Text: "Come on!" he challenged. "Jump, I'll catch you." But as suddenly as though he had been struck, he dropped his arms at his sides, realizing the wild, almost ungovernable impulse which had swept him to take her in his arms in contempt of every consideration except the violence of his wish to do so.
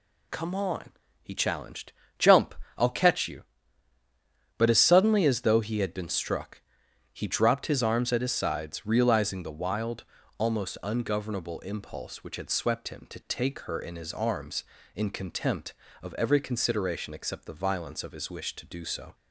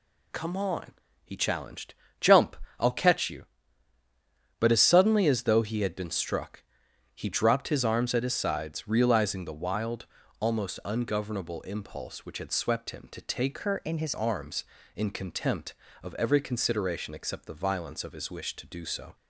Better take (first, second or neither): first